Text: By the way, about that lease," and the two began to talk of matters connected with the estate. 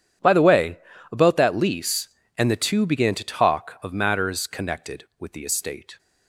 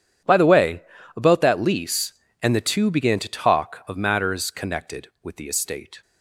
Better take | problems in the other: neither | none

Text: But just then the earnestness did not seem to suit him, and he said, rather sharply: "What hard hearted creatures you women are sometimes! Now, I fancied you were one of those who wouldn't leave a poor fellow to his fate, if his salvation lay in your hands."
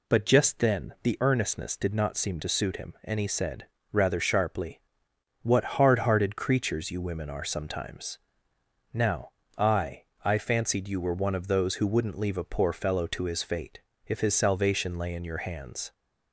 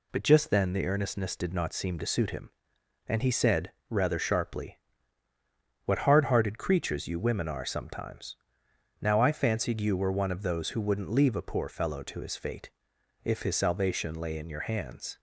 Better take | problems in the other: second | says "I" twice; at 10.2 s

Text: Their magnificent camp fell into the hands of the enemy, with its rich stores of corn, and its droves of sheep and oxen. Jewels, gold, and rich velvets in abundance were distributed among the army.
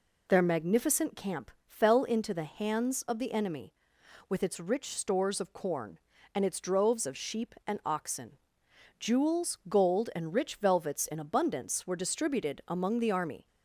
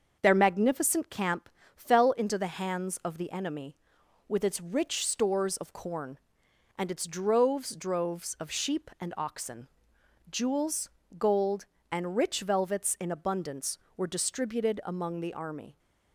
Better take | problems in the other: first | starts louder than the rest; until 1.2 s; 6.5 dB // pauses between "camp" and "fell"; slight; at 1.4 s; 0.28 s long; slight in the first // says "droves" twice; at 7.7 s

